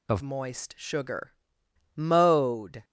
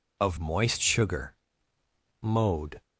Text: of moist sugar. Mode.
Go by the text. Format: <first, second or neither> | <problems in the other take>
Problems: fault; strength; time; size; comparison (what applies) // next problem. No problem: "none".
second | changes voice at "moist"; from 0.2 s on; 2.6 s long